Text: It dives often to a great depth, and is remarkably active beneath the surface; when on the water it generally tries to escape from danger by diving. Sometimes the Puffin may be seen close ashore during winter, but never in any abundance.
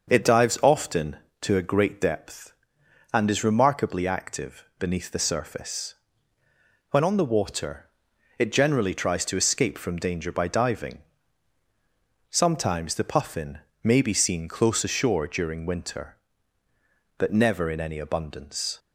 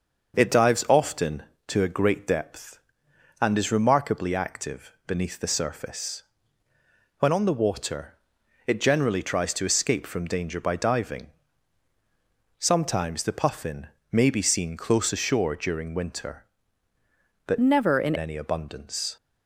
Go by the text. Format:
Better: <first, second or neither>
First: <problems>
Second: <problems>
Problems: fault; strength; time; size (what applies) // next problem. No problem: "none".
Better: first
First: starts louder than the rest; until 1.1 s; 6 dB // pauses between "active" and "beneath"; slight; at 4.6 s; 0.16 s long // pauses between "water" and "it"; noticeable; at 7.8 s; 0.50 s long // pauses between "Puffin" and "may"; slight; at 13.5 s; 0.24 s long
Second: starts louder than the rest; until 1.4 s; 6 dB // pauses between "active" and "beneath"; slight; at 4.9 s; 0.16 s long // pauses between "water" and "it"; noticeable; at 8.1 s; 0.50 s long // pauses between "Puffin" and "may"; slight; at 13.8 s; 0.24 s long // changes voice from "never" to "in"; from 17.6 to 18.1 s; 0.5 s long